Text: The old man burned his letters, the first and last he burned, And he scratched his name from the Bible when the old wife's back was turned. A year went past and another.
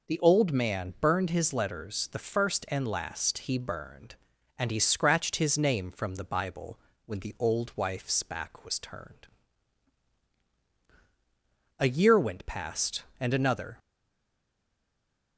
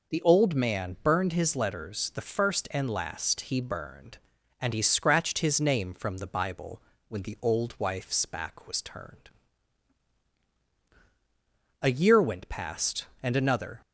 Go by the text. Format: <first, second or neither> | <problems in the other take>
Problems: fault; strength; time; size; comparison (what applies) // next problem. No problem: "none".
second | pauses between "Bible" and "when"; slight; at 6.7 s; 0.28 s long; slight in the second // stays silent after the last word; noticeable; from 13.7 s on; 1.6 s long